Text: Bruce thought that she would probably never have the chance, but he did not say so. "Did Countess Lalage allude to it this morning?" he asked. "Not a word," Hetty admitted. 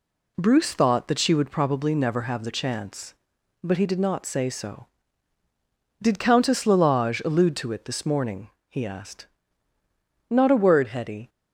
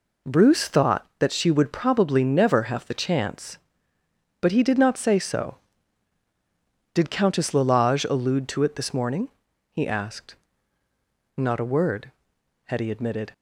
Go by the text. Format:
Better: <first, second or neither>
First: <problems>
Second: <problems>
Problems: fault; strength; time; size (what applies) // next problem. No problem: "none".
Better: second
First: stops before "admitted"; at 11.2 s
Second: none